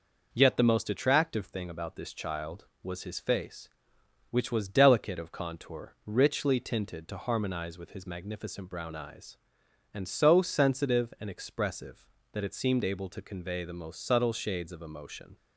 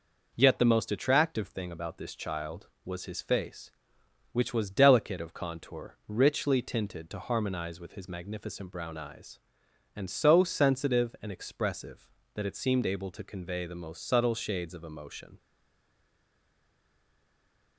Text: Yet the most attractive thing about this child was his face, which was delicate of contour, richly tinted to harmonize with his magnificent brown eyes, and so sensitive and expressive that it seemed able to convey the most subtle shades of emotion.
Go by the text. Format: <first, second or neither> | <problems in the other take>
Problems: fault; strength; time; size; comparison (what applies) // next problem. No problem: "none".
first | stays silent after the last word; from 15.3 s on; 2.4 s long